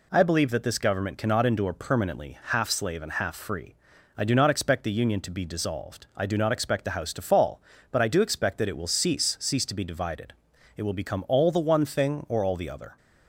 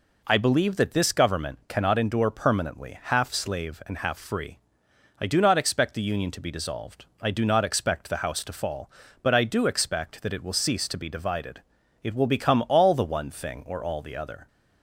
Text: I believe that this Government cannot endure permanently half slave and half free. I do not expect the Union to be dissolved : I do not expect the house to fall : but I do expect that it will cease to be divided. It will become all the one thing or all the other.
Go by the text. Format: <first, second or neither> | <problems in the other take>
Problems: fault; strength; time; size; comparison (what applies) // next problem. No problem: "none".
second | says "cease" twice; at 9.3 s